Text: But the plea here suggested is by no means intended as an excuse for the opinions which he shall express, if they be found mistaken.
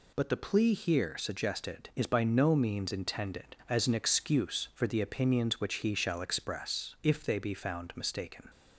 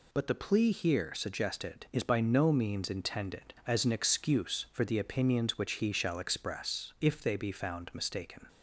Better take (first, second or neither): neither